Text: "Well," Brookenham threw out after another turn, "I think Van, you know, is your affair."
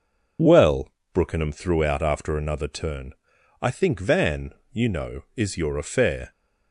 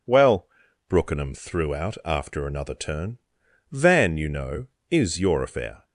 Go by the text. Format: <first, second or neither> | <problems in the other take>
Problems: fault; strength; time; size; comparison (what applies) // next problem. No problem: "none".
first | skips "I think"; at 3.4 s